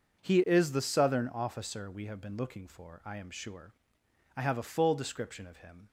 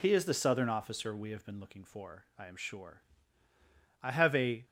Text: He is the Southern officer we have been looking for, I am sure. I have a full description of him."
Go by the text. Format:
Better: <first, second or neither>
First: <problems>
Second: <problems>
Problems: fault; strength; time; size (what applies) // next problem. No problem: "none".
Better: first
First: none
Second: stops before "full description of him"; at 4.6 s